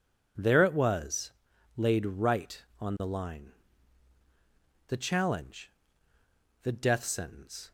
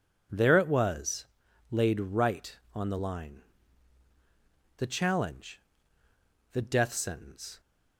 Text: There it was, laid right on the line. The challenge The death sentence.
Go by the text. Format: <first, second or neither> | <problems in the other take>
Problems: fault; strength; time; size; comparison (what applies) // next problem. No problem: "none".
neither | pauses between "challenge" and "The"; noticeable; the same in both